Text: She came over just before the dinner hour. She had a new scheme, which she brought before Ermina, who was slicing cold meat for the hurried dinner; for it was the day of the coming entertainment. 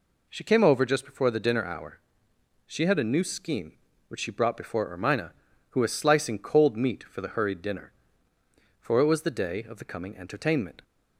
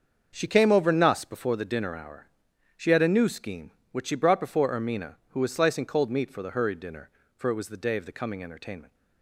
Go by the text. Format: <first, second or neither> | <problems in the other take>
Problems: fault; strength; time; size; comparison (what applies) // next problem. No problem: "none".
first | starts louder than the rest; until 1.3 s; 6.5 dB // says "nuss" for "just"; at 0.8 s